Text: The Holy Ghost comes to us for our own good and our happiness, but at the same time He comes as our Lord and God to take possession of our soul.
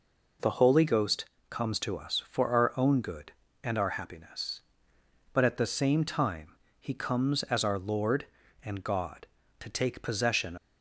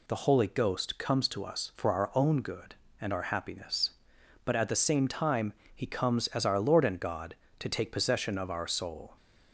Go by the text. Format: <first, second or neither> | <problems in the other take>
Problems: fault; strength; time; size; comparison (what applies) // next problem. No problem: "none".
second | pauses between "Ghost" and "comes"; slight; at 1.2 s; 0.26 s long // pauses between "time" and "He"; slight; at 6.5 s; 0.24 s long; slight in the second // stops before "of our soul"; at 10.5 s